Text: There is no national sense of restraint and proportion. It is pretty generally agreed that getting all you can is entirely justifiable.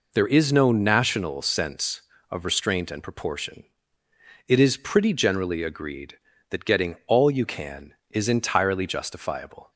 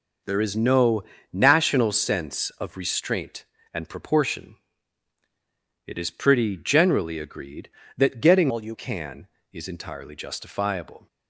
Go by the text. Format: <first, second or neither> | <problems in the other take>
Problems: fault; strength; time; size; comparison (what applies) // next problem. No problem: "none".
first | pauses between "no" and "national"; slight; at 1.0 s; 0.30 s long // changes voice from "all" to "you"; from 8.4 to 8.7 s; 0.3 s long